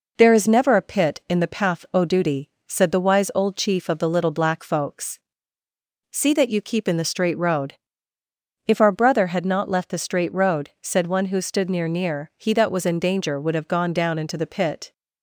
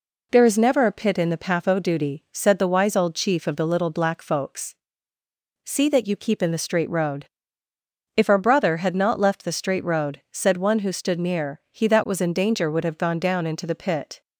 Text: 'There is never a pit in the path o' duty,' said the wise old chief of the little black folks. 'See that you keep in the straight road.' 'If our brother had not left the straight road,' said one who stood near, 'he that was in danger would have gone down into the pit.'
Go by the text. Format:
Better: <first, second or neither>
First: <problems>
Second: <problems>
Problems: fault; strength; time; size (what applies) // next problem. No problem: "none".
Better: second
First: says "near" twice; at 11.8 s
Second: none